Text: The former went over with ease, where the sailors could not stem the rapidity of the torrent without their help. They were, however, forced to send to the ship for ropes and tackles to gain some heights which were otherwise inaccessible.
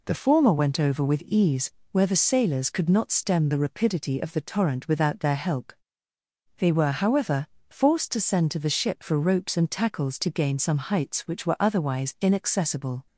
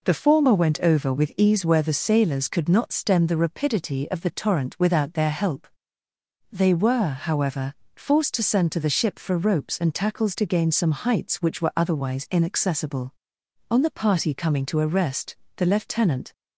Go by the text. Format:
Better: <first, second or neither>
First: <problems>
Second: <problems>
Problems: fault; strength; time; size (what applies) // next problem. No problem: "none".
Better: first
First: none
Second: goes on to say "On the party coming to a rest the Lieutenant"; strong; from 13.7 s on; 2.6 s long